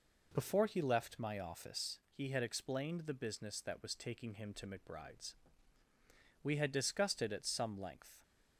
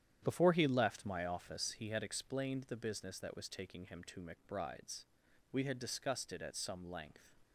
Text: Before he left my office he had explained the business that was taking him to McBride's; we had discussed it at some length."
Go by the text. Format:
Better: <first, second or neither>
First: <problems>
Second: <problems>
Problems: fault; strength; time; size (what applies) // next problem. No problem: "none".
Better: first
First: none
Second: starts louder than the rest; strong; until 1.8 s; 10 dB